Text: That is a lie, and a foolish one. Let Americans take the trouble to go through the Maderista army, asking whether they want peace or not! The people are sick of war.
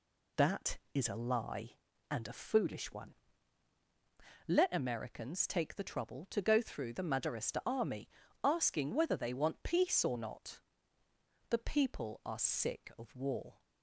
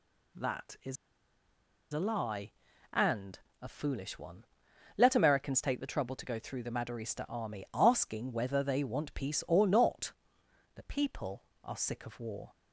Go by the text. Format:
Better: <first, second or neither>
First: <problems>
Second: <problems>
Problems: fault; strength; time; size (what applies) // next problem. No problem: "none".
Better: first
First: none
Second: pauses between "is" and "a"; noticeable; at 0.9 s; 0.96 s long // pauses between "and" and "a"; slight; at 3.3 s; 0.22 s long